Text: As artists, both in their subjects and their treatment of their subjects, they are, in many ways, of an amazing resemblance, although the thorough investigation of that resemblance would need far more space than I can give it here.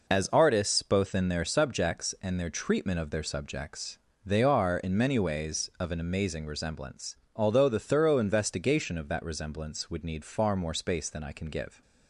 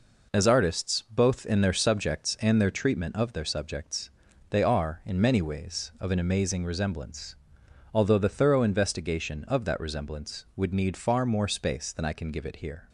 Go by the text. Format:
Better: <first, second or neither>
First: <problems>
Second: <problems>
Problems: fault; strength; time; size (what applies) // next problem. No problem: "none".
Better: second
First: stops before "it here"; at 11.8 s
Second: none